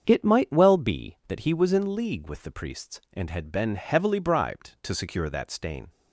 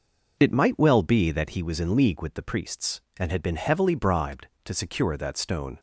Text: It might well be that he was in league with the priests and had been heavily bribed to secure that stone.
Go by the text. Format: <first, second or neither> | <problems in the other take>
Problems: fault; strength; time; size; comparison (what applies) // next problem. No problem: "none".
second | starts louder than the rest; strong; until 1.0 s; 7 dB // says "stain" for "stone"; at 5.4 s